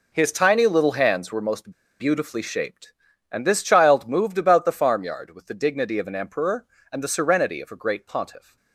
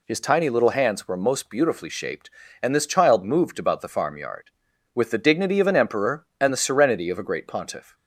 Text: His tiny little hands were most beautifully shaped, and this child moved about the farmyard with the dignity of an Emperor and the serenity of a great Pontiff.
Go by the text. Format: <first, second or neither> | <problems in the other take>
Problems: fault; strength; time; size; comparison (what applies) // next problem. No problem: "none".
second | pauses between "most" and "beautifully"; slight; at 1.7 s; 0.28 s long